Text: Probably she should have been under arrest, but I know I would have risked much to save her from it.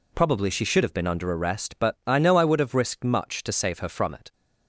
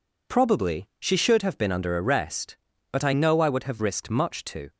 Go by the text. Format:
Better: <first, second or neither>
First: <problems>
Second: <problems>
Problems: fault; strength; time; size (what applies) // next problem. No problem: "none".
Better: first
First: none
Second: stops before "save her from it"; at 4.7 s